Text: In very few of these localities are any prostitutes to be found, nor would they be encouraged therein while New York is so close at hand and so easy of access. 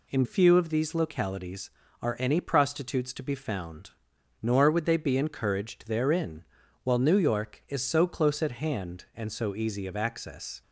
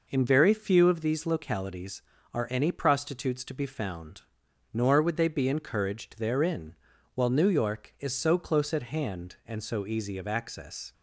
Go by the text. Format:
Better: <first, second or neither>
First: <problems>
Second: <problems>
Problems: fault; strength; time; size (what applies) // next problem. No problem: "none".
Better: second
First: skips "very"; at 0.2 s // pauses between "therein" and "while"; at 6.4 s; 0.40 s long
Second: pauses between "therein" and "while"; at 6.7 s; 0.40 s long